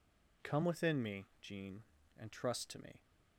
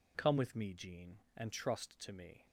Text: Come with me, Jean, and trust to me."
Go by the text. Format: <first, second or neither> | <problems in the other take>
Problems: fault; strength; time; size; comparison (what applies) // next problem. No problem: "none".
second | says "within" for "with"; at 0.6 s